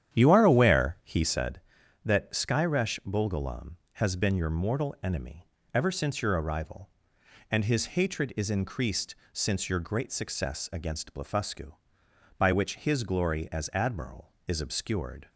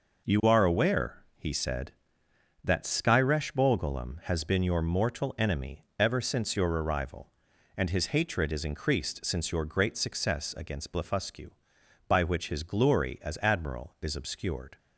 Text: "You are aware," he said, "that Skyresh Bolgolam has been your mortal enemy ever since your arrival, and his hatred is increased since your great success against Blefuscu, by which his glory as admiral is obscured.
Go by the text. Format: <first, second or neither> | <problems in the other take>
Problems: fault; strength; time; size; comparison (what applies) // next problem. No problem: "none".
second | starts louder than the rest; strong; until 1.6 s; 9.5 dB // pauses between "enemy" and "ever"; slight; at 5.4 s; 0.24 s long // pauses between "increased" and "since"; slight; at 9.1 s; 0.16 s long